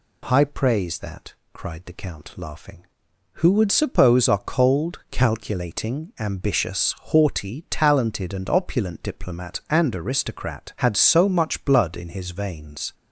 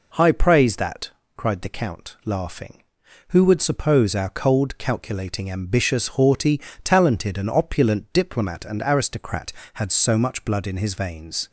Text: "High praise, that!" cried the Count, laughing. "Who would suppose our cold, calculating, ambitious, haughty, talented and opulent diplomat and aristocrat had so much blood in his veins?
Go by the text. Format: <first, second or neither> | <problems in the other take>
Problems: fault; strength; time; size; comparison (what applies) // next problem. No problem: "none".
neither | none